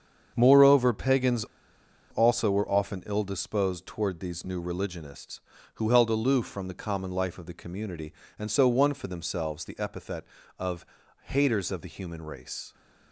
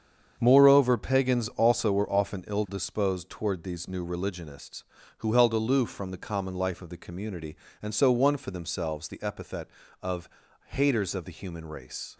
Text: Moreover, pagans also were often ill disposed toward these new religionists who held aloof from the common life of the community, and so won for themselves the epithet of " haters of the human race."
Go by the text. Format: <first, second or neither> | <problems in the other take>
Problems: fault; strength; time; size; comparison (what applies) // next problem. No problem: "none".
second | starts louder than the rest; strong; until 1.3 s; 7.5 dB; strong in the second // pauses between "pagans" and "also"; noticeable; at 1.4 s; 0.66 s long